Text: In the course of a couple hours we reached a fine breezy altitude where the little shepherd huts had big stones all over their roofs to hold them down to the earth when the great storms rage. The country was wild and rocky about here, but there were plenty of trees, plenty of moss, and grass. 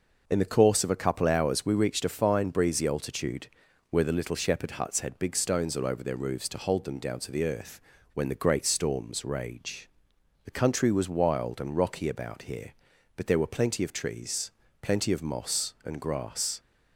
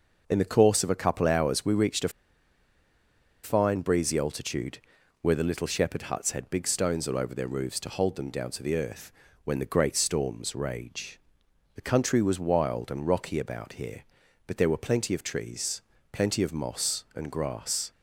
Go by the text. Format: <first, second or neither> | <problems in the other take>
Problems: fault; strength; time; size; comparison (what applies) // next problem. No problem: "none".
first | pauses between "a" and "fine"; strong; at 2.0 s; 1.3 s long // pauses between "altitude" and "where"; noticeable; at 4.7 s; 0.46 s long; noticeable in the first // pauses between "earth" and "when"; slight; at 9.1 s; 0.34 s long; slight in the first